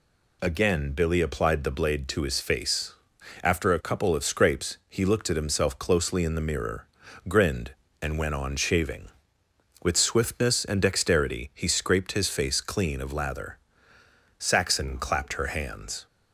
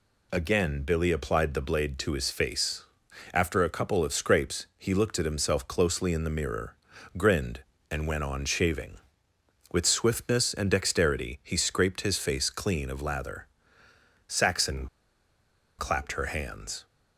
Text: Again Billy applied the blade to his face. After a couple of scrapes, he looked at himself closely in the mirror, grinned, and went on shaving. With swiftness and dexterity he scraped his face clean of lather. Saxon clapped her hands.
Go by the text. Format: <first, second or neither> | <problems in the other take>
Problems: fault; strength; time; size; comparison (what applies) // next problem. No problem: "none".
first | pauses between "Saxon" and "clapped"; noticeable; at 14.8 s; 0.92 s long